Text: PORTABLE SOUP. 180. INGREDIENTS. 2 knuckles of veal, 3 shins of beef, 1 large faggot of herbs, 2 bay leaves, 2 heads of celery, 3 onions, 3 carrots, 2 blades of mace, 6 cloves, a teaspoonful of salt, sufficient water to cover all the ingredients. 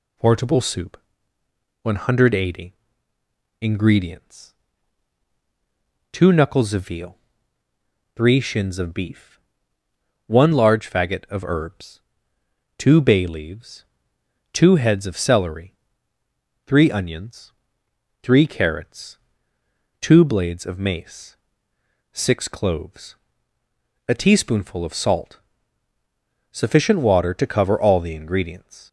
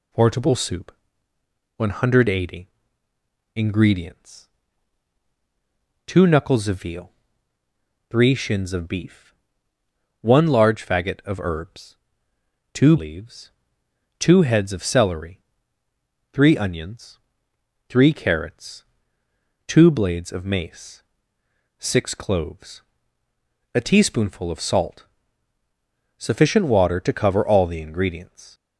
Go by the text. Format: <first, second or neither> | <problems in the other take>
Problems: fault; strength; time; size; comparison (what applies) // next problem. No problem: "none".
first | skips "bay"; at 12.9 s